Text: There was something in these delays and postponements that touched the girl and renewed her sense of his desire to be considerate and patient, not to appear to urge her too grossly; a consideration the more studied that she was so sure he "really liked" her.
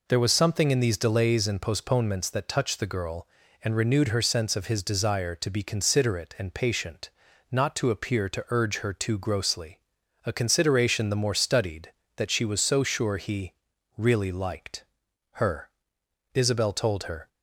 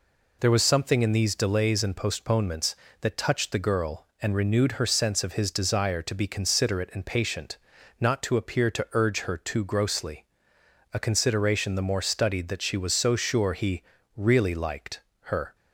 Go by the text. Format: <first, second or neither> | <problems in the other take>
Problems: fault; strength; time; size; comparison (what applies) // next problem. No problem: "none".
second | pauses between "he" and "really"; at 13.5 s; 0.44 s long; slight in the second // pauses between "liked" and "her"; noticeable; at 14.8 s; 0.48 s long; slight in the second // goes on to say "Isabel told her"; noticeable; from 16.3 s on; 0.92 s long